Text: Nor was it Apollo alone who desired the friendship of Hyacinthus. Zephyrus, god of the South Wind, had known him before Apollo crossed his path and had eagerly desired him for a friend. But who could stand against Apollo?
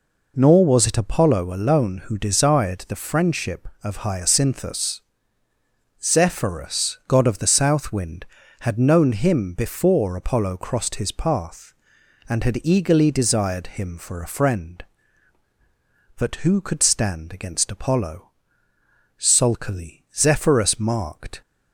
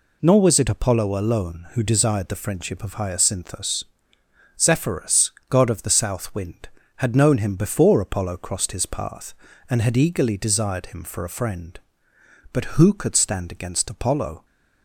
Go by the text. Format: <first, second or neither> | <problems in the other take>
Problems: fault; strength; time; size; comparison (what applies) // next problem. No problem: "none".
second | goes on to say "Sulkily Zephyrus marked"; strong; from 19.1 s on; 2.2 s long